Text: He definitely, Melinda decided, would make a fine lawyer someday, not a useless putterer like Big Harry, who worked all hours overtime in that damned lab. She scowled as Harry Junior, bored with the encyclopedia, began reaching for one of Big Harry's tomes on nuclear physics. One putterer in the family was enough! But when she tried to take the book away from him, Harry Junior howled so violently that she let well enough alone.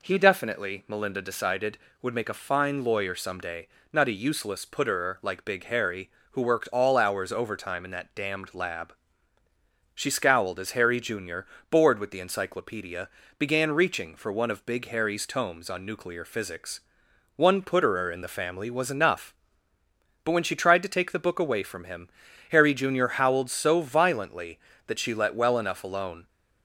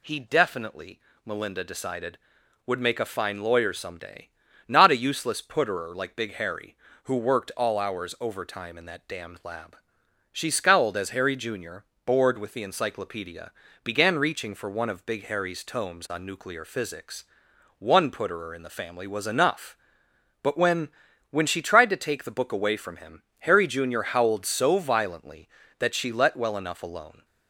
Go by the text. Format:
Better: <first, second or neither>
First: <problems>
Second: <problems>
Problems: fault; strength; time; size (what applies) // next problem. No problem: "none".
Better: first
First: none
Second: says "when" twice; at 21.3 s